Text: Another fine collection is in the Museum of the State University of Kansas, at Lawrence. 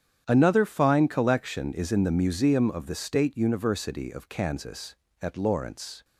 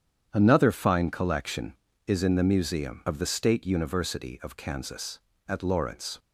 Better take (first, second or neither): neither